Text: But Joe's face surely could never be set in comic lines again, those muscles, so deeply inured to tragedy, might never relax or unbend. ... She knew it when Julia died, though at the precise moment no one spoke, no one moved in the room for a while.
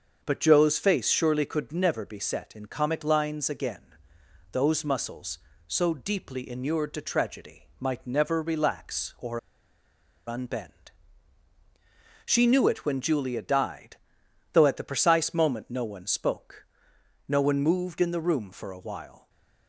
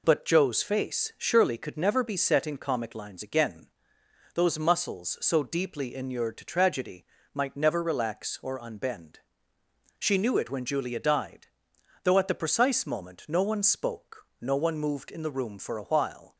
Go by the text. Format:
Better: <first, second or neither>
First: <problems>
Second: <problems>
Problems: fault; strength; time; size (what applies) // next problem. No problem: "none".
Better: second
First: starts louder than the rest; until 1.2 s; 6.5 dB // pauses between "or" and "unbend"; noticeable; at 9.3 s; 0.87 s long // stays silent after the last word; slight; from 19.1 s on; 0.5 s long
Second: none